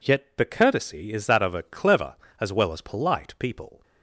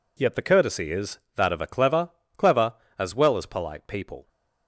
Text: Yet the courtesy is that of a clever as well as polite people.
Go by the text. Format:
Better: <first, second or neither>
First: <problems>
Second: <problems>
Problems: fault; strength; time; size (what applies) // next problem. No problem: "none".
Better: first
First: none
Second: says "clever" twice; at 2.3 s